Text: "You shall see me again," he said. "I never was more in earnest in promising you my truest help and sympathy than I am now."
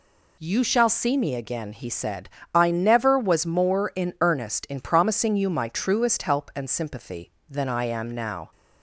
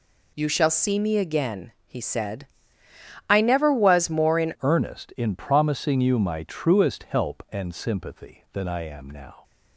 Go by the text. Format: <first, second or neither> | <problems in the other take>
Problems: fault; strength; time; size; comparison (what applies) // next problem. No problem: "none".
first | changes voice at "earnest"; from 4.6 s on; 4.8 s long